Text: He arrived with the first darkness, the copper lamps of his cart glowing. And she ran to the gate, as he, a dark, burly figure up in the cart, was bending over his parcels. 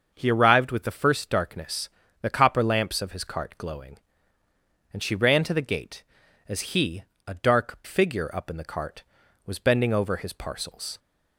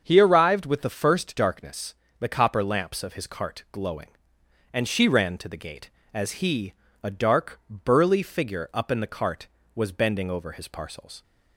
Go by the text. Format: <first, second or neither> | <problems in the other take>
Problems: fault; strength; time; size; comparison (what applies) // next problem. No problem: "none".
second | starts louder than the rest; until 1.1 s; 6.5 dB; also in the second // skips "burly"; at 7.8 s